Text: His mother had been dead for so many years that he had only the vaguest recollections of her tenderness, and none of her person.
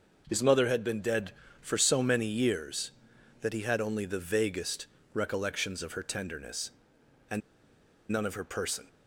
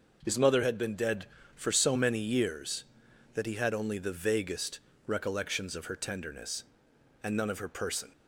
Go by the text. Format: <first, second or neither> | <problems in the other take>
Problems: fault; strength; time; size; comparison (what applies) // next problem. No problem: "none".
second | pauses between "vaguest" and "recollections"; slight; at 4.8 s; 0.26 s long; slight in the second // pauses between "and" and "none"; noticeable; at 7.4 s; 0.70 s long